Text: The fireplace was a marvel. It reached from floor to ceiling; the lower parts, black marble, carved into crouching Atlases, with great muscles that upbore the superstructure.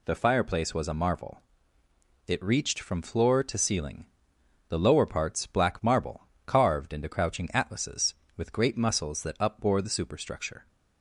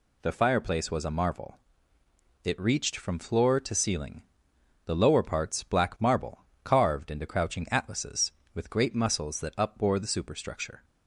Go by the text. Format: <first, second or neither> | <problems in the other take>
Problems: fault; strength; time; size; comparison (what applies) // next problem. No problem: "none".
neither | none